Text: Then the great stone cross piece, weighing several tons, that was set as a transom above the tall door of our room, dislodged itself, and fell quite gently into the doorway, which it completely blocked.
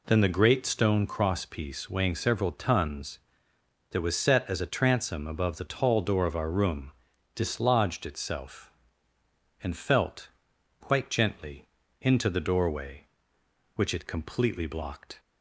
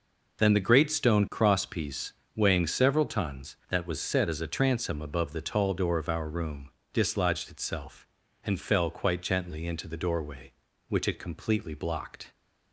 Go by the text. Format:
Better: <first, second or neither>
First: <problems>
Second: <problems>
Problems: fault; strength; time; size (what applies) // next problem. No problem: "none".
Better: second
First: says "felt" for "fell"; at 9.7 s // pauses between "gently" and "into"; slight; at 11.6 s; 0.34 s long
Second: none